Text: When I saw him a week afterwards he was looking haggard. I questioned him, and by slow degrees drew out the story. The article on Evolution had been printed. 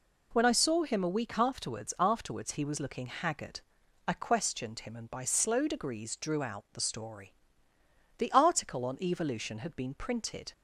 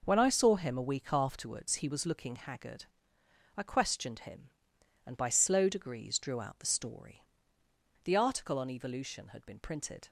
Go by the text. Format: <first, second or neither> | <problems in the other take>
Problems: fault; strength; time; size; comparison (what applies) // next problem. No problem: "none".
second | says "afterwards" twice; at 1.9 s